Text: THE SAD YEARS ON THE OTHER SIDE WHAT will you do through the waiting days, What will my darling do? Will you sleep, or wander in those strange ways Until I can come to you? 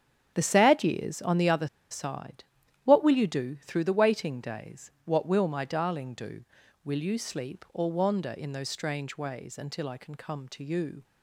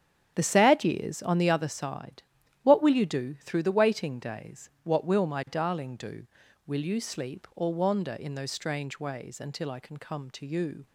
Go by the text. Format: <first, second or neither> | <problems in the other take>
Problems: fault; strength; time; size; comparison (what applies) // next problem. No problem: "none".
second | starts louder than the rest; strong; until 1.4 s; 9 dB; strong in the second // pauses between "OTHER" and "SIDE"; slight; at 1.6 s; 0.23 s long // pauses between "SIDE" and "WHAT"; at 2.4 s; 0.40 s long; also in the second